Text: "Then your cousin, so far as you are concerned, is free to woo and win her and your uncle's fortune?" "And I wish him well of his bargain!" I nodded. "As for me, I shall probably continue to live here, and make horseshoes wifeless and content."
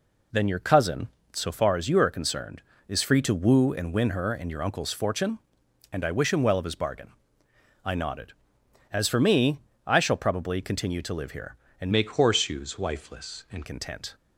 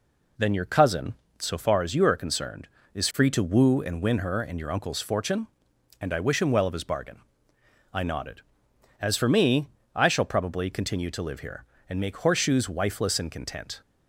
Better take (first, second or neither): second